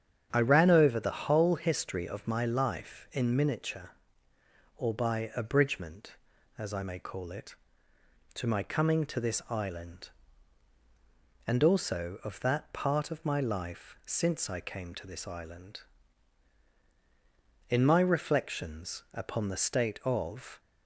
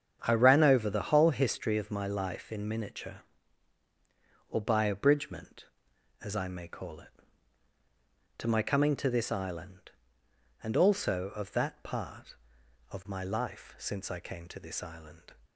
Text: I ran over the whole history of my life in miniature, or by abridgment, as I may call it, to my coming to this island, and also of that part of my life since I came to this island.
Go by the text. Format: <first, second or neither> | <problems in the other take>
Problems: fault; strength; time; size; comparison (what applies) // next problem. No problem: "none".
second | starts louder than the rest; strong; until 1.3 s; 8 dB; strong in the second // goes on to say "In my reflections upon the state of"; strong; from 17.6 s on; 2.9 s long